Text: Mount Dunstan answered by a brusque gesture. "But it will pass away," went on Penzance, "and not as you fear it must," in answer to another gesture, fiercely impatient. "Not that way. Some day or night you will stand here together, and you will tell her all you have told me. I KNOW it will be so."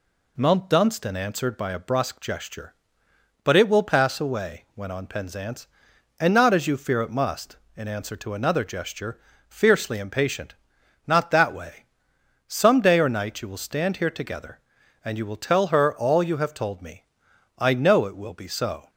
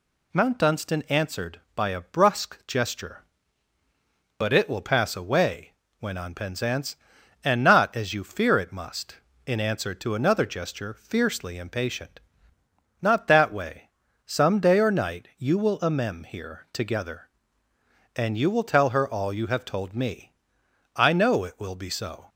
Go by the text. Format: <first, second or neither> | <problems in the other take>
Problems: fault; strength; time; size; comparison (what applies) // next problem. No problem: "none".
first | says "amem" for "stand"; at 15.8 s